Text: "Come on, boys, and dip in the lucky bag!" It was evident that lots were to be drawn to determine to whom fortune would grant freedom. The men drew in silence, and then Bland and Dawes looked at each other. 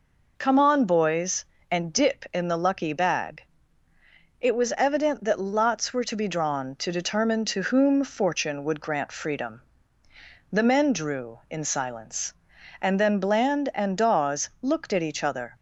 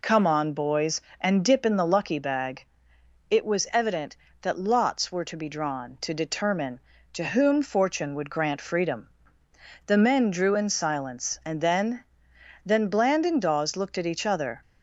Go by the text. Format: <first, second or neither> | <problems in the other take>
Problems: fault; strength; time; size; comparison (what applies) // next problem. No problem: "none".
first | says "then" twice; at 12.6 s